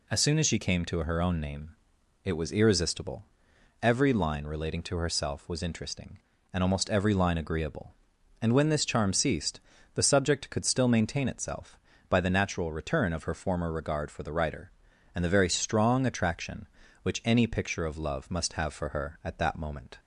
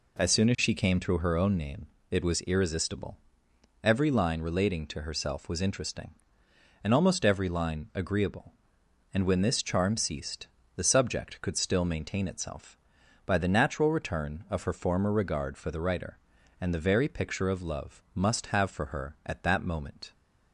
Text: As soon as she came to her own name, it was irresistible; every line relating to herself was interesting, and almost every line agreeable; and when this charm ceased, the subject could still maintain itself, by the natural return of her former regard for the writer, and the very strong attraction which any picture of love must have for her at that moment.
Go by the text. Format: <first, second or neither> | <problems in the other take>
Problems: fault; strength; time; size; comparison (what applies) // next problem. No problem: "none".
first | skips "strong attraction which any"; at 17.0 s